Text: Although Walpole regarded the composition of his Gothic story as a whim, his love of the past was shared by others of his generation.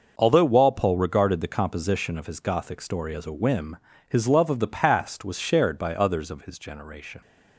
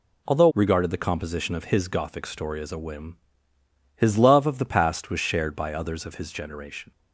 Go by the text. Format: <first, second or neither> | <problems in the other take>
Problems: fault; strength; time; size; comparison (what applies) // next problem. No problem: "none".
first | skips "Walpole"; at 0.5 s